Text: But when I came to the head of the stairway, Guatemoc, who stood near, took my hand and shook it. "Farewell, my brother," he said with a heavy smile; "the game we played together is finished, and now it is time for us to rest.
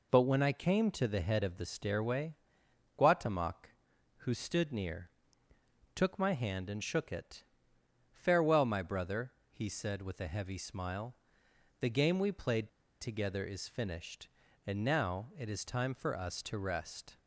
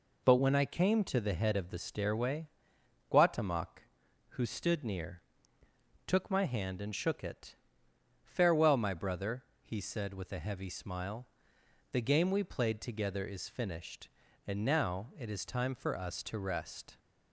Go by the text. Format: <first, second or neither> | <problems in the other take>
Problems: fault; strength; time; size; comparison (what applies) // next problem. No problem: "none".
second | pauses between "played" and "together"; slight; at 12.6 s; 0.32 s long